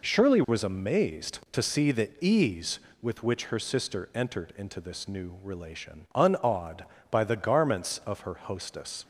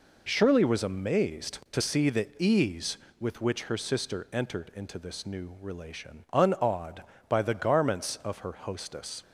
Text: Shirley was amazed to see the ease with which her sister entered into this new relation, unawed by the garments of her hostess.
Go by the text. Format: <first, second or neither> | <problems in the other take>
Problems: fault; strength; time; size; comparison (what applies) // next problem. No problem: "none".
neither | none